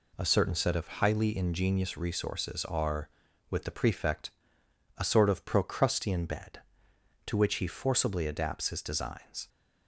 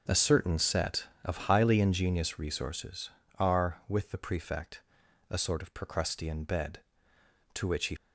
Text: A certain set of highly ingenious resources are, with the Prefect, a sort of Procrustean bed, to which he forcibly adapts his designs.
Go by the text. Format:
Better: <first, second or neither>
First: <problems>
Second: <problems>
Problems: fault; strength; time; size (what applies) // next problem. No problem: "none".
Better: first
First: none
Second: starts louder than the rest; until 1.2 s; 6 dB // stops before "forcibly adapts his designs"; at 7.9 s